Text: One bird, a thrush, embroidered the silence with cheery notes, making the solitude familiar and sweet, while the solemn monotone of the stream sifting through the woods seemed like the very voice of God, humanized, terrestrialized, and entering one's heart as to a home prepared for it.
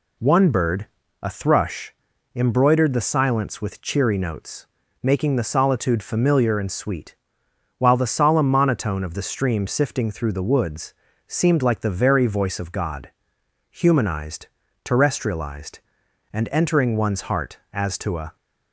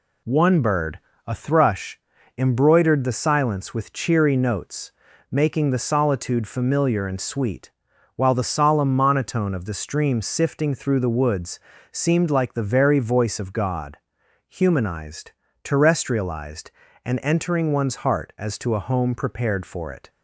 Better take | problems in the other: second | pauses between "woods" and "seemed"; slight; at 10.9 s; 0.34 s long; slight in the second // stops before "home prepared for it"; at 18.3 s

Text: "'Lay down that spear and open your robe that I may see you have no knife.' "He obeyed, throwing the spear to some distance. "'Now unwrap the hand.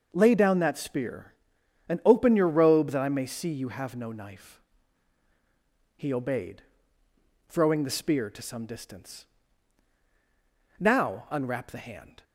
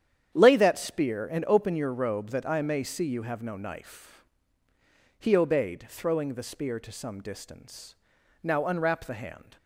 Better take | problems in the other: first | starts louder than the rest; strong; until 1.3 s; 9 dB; noticeable in the first // skips "down"; at 0.5 s

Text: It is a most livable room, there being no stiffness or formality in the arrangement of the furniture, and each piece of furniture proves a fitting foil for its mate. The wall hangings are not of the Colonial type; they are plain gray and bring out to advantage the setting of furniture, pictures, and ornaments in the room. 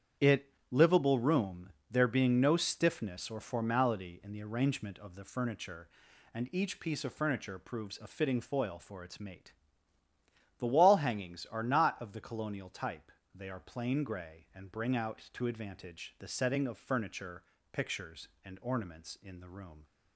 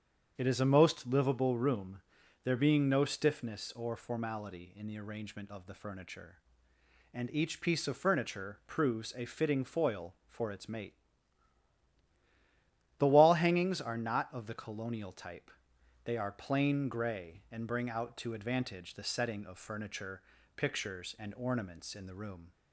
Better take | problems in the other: second | starts louder than the rest; strong; until 1.3 s; 8.5 dB; strong in the second // skips "is a most"; at 0.6 s

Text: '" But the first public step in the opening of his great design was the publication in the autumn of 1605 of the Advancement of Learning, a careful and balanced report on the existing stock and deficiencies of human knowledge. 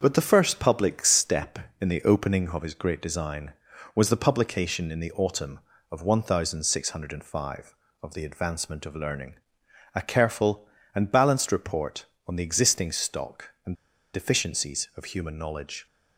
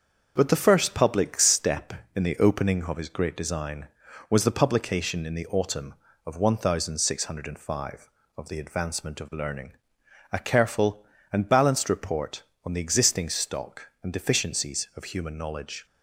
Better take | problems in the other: second | starts louder than the rest; until 1.0 s; 6.5 dB; also in the second // pauses between "and" and "deficiencies"; at 13.7 s; 0.38 s long

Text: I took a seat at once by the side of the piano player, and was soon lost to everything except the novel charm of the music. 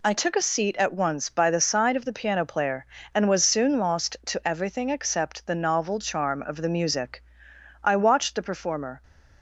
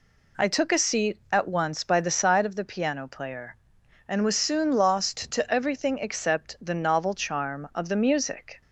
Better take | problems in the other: second | goes on to say "I watched the performer"; noticeable; from 7.8 s on; 1.2 s long

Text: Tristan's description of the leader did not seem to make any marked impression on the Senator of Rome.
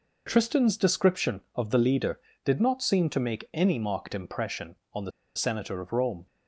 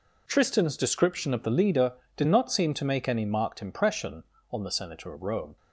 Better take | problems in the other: second | pauses between "the" and "Senator"; slight; at 5.1 s; 0.25 s long

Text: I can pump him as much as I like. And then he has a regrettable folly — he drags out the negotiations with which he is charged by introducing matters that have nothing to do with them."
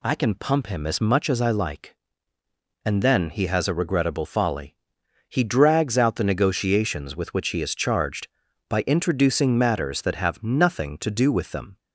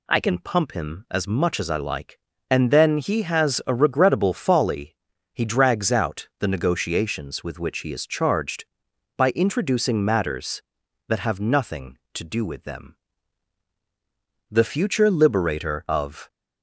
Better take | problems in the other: first | goes on to say "The future liberator of"; strong; from 14.5 s on; 1.8 s long

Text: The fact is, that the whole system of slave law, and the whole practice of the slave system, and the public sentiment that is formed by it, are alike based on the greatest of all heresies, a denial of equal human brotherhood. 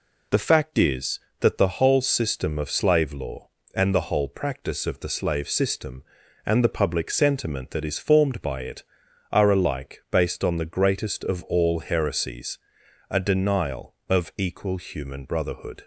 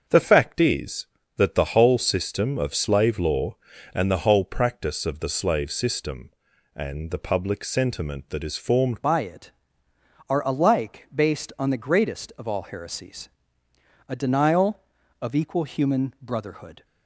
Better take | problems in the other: first | starts louder than the rest; until 1.4 s; 6.5 dB // changes voice at "by"; from 9.0 s on; 7.8 s long

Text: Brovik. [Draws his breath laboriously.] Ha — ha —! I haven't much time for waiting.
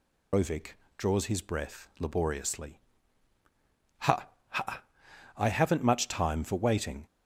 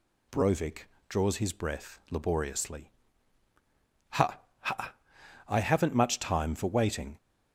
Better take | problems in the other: second | loses the start of "Brovik"; at 0.3 s; 135 ms

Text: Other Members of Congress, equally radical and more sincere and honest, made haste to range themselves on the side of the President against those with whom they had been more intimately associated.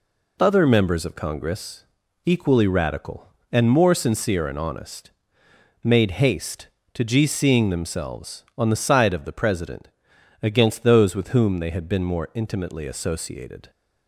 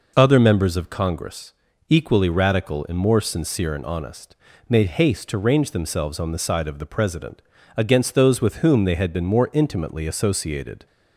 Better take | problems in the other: second | says "gcing" for "range"; at 7.0 s // pauses between "President" and "against"; noticeable; at 9.8 s; 0.52 s long; slight in the second

